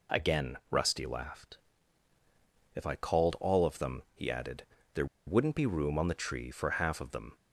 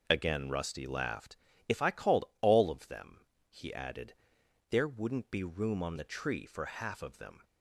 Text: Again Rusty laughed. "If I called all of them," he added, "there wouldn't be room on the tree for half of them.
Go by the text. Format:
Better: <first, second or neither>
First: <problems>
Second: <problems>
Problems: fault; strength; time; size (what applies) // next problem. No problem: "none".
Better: second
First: pauses between "there" and "wouldn't"; slight; at 5.0 s; 0.20 s long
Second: none